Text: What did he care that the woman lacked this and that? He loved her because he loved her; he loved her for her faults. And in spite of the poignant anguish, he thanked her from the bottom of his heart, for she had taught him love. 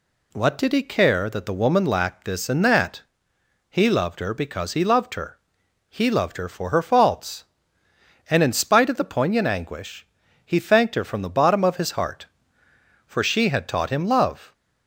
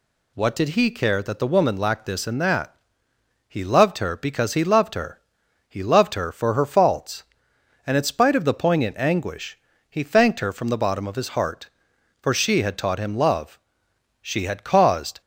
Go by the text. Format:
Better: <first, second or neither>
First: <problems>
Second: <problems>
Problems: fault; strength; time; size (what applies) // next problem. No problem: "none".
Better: first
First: none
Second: goes on to say "She had caused"; noticeable; from 14.2 s on; 1.0 s long